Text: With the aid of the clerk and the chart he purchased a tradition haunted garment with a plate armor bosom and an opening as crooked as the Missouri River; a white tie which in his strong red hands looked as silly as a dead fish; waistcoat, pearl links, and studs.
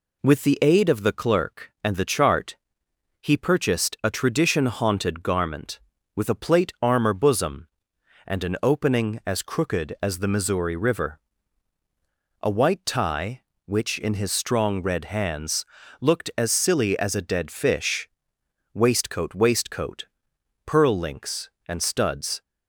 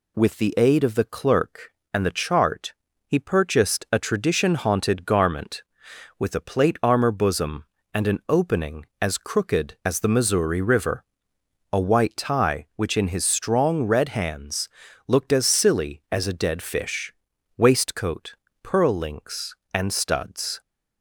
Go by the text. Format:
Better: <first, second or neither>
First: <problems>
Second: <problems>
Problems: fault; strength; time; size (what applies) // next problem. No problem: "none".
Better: second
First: pauses between "chart" and "he"; noticeable; at 2.5 s; 0.64 s long // pauses between "hands" and "looked"; slight; at 15.6 s; 0.36 s long // says "waistcoat" twice; at 19.3 s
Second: pauses between "chart" and "he"; slight; at 2.7 s; 0.36 s long // pauses between "hands" and "looked"; at 14.6 s; 0.40 s long